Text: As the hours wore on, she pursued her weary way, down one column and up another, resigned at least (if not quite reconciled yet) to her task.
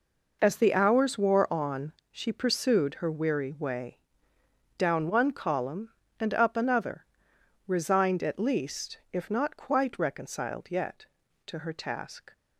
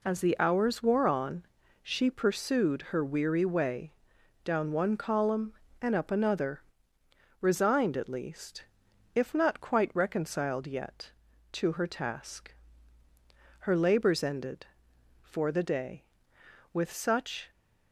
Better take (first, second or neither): first